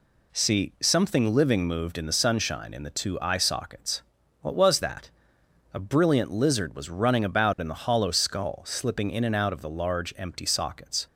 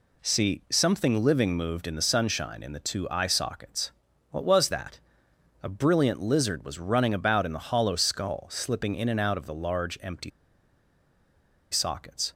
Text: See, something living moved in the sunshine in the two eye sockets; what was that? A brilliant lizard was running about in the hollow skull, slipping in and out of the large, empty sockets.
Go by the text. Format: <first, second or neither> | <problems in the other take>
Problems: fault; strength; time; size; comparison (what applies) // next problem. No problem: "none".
first | pauses between "empty" and "sockets"; strong; at 10.3 s; 1.4 s long